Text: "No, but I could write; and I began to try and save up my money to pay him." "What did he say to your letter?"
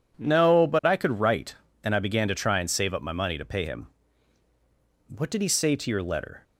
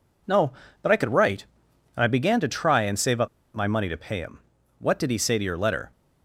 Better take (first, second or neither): first